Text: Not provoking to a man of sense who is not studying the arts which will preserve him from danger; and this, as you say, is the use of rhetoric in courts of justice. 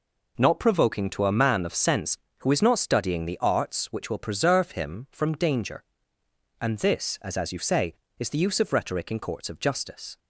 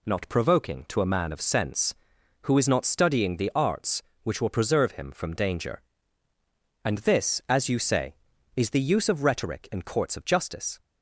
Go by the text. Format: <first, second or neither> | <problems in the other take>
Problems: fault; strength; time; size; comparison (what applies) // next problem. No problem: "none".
second | says "as" twice; at 7.3 s